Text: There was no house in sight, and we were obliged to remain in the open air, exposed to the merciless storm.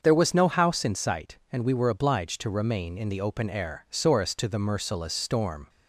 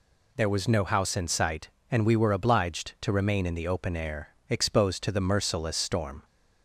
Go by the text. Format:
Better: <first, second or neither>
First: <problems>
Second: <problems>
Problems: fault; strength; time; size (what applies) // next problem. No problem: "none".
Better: second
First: starts louder than the rest; until 1.0 s; 6.5 dB // says "sorest" for "exposed"; at 3.8 s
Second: none